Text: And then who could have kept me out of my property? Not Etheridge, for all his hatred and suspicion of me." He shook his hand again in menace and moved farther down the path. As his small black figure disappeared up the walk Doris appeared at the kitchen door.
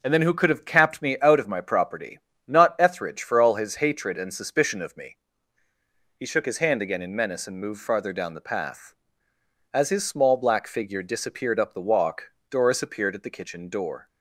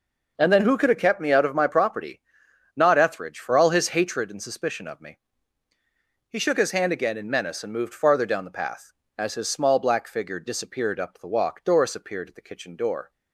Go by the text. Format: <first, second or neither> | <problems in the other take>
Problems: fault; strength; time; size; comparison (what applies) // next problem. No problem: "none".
second | says "capped" for "kept"; at 0.6 s // pauses between "walk" and "Doris"; slight; at 12.3 s; 0.16 s long